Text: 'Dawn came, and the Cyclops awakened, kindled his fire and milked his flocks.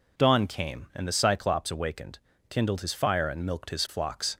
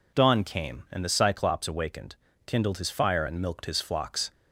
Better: neither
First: none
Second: none

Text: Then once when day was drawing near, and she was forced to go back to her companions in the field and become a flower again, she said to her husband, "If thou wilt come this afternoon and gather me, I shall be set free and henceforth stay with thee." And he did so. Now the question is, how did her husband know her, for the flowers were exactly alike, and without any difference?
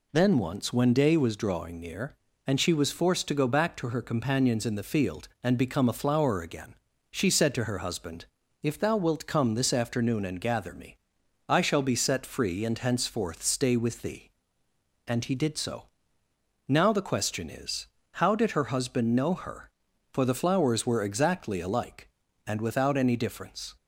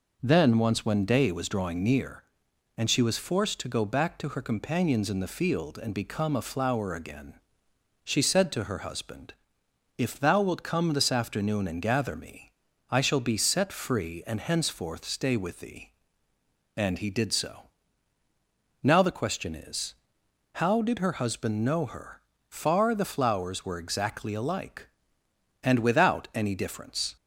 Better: first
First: none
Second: says "far" for "for"; at 22.4 s

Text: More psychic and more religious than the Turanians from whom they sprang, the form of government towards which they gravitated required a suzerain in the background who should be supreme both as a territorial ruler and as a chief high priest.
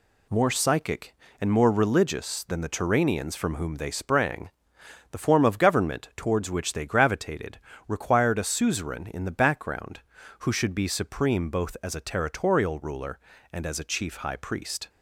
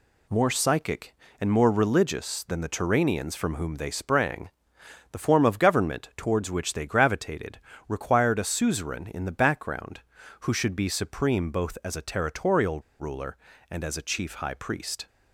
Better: first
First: pauses between "gravitated" and "required"; slight; at 7.5 s; 0.28 s long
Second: pauses between "gravitated" and "required"; slight; at 7.5 s; 0.28 s long // pauses between "territorial" and "ruler"; slight; at 12.7 s; 0.19 s long

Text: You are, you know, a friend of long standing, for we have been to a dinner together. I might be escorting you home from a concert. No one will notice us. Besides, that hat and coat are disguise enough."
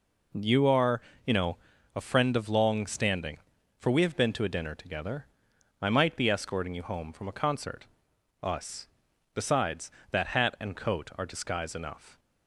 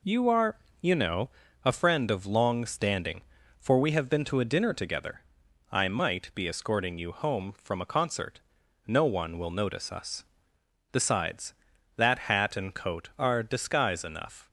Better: second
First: skips "No one will notice"; at 8.1 s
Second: none

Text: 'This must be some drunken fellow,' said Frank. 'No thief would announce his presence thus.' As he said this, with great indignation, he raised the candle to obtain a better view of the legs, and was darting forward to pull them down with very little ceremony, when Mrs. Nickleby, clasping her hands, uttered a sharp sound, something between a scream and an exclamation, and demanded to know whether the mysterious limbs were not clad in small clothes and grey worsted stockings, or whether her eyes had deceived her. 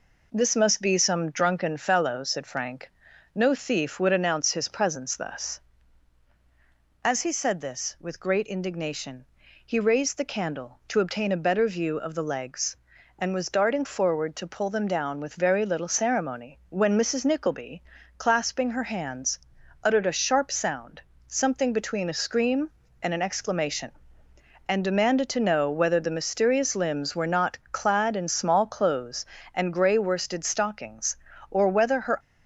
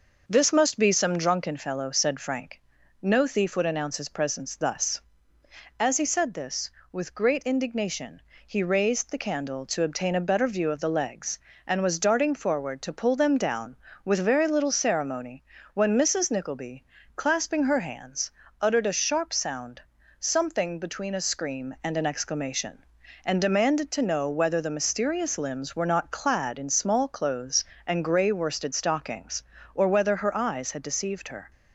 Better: second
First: stops before "eyes had deceived her"; at 32.1 s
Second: none

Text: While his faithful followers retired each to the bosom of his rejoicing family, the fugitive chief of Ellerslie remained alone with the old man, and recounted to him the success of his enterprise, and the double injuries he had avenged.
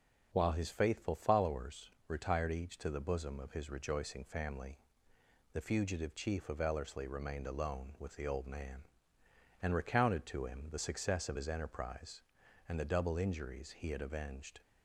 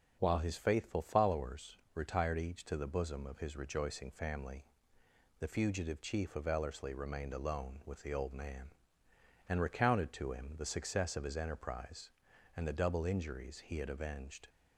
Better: neither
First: pauses between "followers" and "retired"; slight; at 1.9 s; 0.18 s long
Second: pauses between "followers" and "retired"; slight; at 1.7 s; 0.18 s long

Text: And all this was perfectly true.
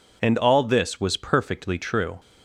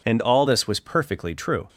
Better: first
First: none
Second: changes voice at "this"; from 0.4 s on; 1.2 s long

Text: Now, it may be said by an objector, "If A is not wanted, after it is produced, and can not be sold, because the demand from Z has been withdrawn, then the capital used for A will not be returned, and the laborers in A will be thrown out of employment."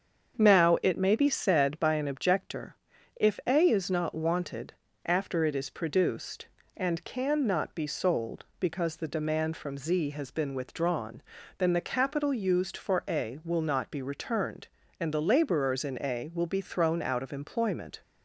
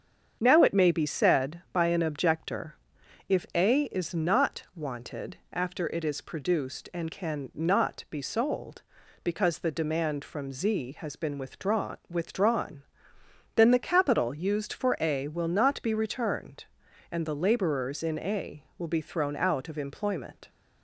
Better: first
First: starts louder than the rest; until 1.4 s; 7 dB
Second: starts louder than the rest; strong; until 1.4 s; 7.5 dB // says "withdrawn" twice; at 12.0 s

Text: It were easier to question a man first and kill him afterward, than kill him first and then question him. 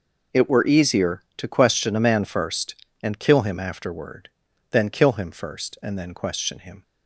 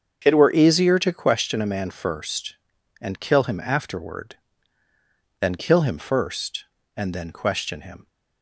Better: first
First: none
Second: starts louder than the rest; until 1.5 s; 7 dB

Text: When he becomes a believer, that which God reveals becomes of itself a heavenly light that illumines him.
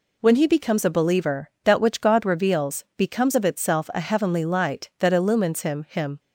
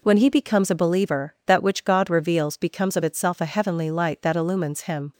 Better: second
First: says "him" twice; at 5.8 s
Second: none

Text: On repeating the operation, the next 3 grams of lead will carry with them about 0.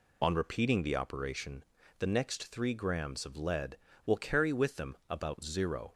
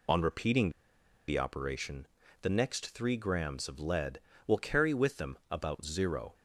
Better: first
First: none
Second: pauses between "repeating" and "the"; noticeable; at 0.6 s; 0.58 s long

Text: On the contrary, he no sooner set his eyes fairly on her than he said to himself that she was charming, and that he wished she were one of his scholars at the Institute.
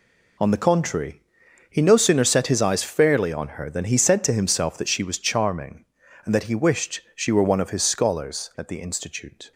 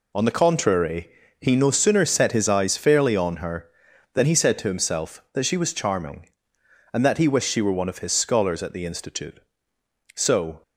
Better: first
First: none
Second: goes on to say "So"; slight; from 10.1 s on; 0.48 s long

